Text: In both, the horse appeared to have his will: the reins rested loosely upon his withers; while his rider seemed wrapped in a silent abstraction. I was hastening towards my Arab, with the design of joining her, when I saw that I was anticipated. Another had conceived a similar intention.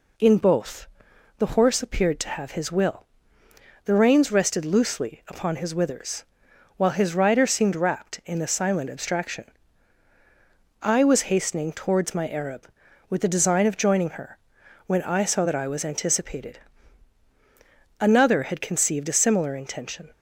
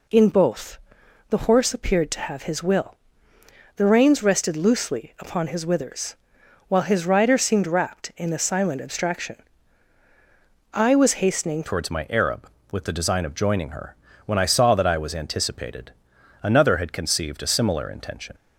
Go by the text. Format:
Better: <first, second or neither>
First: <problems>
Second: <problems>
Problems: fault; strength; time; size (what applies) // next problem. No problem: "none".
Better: first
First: none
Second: changes voice at "towards"; from 11.6 s on; 6.7 s long